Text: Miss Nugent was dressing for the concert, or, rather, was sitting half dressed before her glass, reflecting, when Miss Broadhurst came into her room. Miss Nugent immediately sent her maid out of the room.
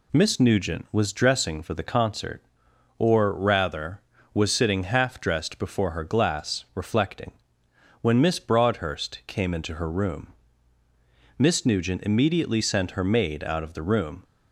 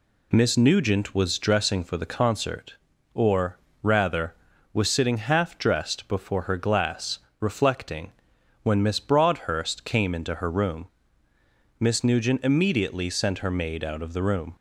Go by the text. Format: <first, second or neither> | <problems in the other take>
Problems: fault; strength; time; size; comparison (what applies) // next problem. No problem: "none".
neither | none